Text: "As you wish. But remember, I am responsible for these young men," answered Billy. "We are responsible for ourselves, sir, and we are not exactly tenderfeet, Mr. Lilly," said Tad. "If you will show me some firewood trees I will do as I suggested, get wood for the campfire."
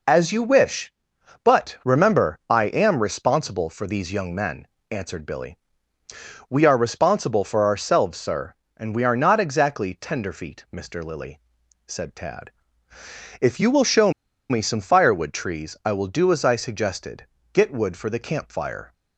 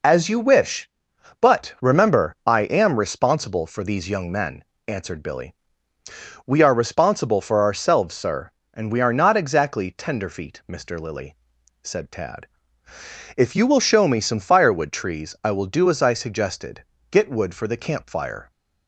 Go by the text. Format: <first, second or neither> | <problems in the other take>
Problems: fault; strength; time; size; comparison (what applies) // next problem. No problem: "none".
second | pauses between "show" and "me"; at 14.1 s; 0.38 s long